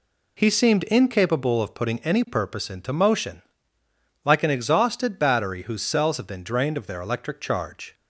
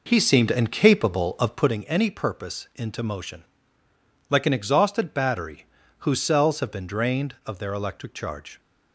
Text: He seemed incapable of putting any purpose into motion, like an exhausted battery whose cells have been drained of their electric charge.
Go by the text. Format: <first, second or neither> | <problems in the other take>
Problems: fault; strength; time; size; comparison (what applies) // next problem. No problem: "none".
first | starts louder than the rest; noticeable; until 1.8 s; 4.5 dB // pauses between "battery" and "whose"; slight; at 5.6 s; 0.34 s long